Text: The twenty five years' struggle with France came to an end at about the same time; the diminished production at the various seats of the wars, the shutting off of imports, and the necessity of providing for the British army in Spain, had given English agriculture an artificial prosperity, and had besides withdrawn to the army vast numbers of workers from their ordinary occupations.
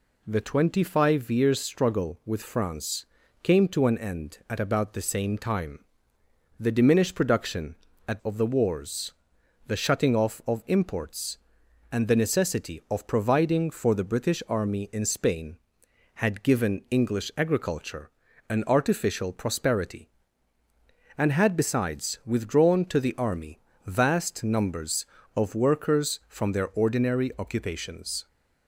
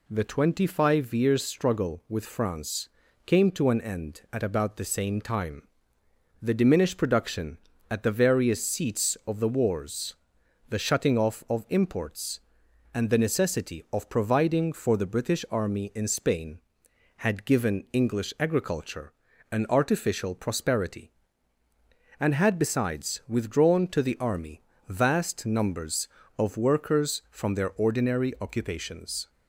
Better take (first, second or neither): second